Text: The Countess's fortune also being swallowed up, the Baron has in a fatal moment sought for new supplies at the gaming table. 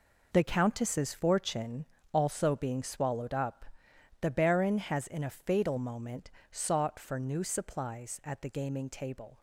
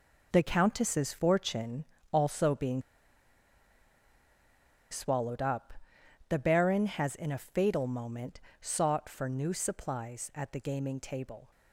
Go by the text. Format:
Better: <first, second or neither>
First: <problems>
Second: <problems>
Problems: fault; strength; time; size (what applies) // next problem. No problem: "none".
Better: first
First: pauses between "fortune" and "also"; slight; at 1.8 s; 0.26 s long // pauses between "moment" and "sought"; slight; at 6.3 s; 0.22 s long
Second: pauses between "fortune" and "also"; slight; at 1.8 s; 0.26 s long // pauses between "being" and "swallowed"; strong; at 2.8 s; 2.0 s long // pauses between "moment" and "sought"; slight; at 8.4 s; 0.22 s long